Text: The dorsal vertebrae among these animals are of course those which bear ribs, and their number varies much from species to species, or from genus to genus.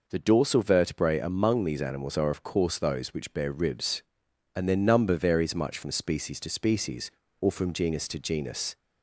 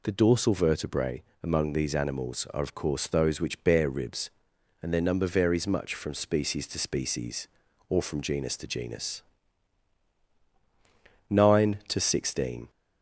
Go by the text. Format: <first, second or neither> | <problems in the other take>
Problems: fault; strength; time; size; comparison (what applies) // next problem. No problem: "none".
first | pauses between "vertebrae" and "among"; slight; at 1.2 s; 0.20 s long // goes on to say "Nine to sixteen"; from 11.2 s on; 1.4 s long